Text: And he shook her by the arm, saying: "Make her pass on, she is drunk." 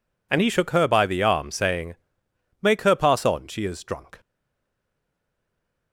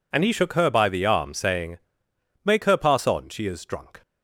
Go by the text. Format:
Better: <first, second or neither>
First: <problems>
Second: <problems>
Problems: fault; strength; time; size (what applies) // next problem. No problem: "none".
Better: second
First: stays silent after the last word; noticeable; from 4.1 s on; 1.8 s long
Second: none